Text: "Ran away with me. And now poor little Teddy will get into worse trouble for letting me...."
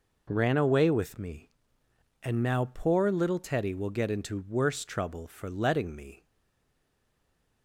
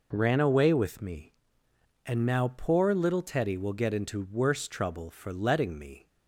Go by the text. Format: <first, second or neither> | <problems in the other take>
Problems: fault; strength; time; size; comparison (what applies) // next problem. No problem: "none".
second | stays silent after the last word; noticeable; from 6.2 s on; 1.4 s long